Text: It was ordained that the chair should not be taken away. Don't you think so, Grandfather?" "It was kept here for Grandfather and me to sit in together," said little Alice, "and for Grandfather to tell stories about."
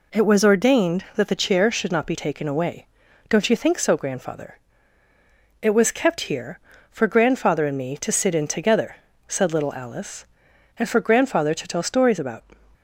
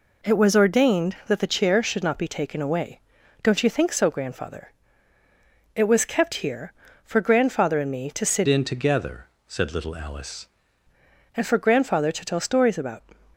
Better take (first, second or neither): first